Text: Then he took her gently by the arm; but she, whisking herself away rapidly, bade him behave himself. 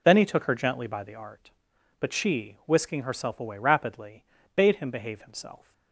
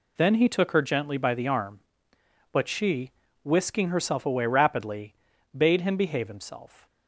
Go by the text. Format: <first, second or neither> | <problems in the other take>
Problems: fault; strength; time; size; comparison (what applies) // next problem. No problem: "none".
second | says "art" for "arm"; at 1.1 s